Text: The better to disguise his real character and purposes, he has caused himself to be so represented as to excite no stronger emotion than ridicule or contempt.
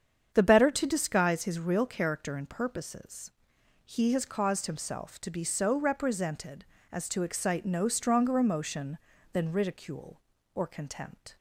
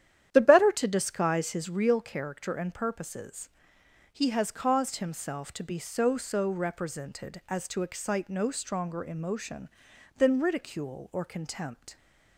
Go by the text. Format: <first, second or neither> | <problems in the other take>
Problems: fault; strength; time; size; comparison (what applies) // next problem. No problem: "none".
first | starts louder than the rest; strong; until 1.3 s; 10.5 dB; strong in the first // says "so" twice; at 6.1 s